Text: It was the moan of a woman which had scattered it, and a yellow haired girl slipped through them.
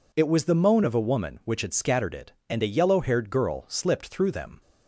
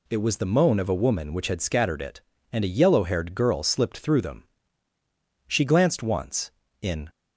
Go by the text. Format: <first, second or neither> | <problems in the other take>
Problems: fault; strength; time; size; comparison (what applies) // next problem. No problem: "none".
first | goes on to say "She glanced once in"; from 5.4 s on; 1.6 s long